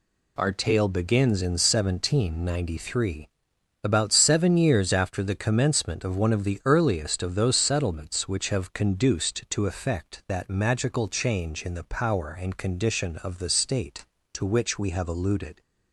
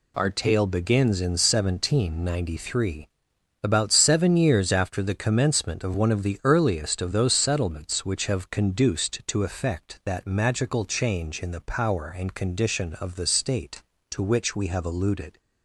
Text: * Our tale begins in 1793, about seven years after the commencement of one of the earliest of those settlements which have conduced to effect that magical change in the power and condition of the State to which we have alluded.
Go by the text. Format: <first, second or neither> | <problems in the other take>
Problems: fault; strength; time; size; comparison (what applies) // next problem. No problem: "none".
neither | none